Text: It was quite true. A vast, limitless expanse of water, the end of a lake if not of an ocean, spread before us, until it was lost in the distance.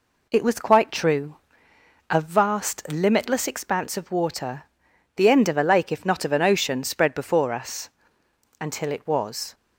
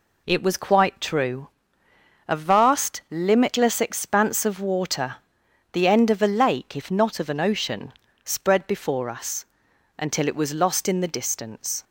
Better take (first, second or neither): second